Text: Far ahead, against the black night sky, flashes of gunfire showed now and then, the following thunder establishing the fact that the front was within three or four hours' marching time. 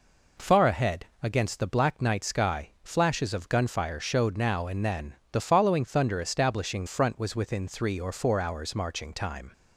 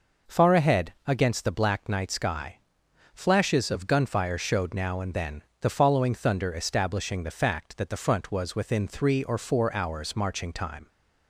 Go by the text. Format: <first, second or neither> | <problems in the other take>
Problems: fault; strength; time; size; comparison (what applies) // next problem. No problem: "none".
second | skips "the fact that the"; at 6.8 s